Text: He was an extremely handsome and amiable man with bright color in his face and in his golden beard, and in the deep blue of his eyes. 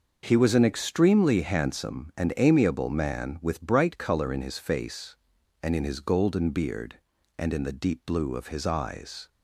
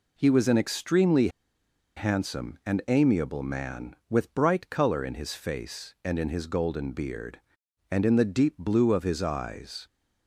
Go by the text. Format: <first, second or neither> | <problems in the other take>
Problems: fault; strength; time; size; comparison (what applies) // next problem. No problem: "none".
first | pauses between "extremely" and "handsome"; noticeable; at 1.2 s; 0.68 s long